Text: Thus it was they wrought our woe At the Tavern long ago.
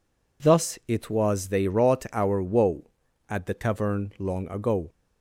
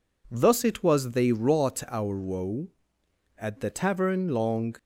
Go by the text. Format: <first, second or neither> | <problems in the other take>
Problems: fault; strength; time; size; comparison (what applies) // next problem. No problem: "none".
first | stops before "ago"; at 4.7 s